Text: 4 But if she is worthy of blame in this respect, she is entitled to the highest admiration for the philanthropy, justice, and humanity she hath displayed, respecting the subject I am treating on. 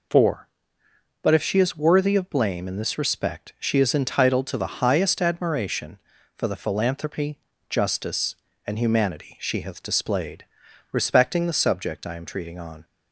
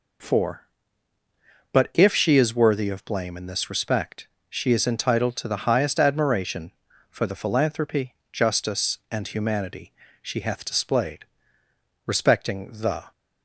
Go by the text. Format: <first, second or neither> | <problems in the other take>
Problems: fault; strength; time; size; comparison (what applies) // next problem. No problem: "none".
first | pauses between "humanity" and "she"; slight; at 9.9 s; 0.28 s long // stops before "subject I am treating on"; at 13.1 s